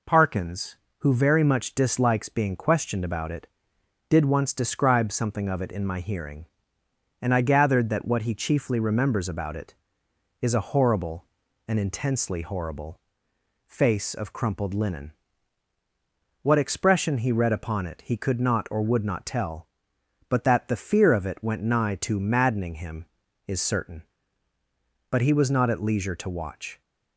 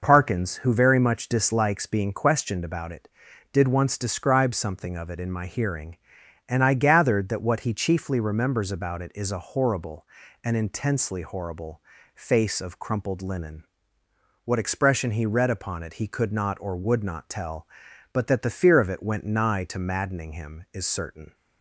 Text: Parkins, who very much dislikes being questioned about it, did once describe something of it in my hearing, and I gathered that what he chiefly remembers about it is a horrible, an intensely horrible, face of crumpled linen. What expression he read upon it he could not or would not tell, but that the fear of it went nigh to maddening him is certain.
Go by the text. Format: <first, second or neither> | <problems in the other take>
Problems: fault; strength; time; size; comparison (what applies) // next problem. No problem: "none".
second | goes on to say "But he was not at leisure to watch"; strong; from 25.0 s on; 1.7 s long